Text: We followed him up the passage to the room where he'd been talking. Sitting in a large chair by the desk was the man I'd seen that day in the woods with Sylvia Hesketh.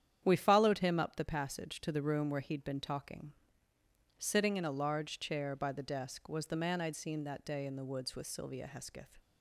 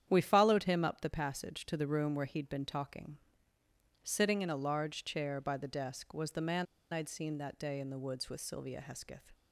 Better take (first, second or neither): first